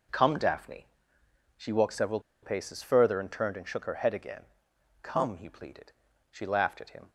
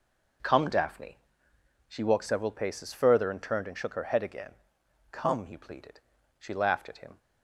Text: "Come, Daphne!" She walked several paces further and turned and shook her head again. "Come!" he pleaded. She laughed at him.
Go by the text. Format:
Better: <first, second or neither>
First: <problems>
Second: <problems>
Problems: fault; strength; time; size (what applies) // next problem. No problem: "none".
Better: second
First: pauses between "several" and "paces"; slight; at 2.1 s; 0.22 s long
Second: none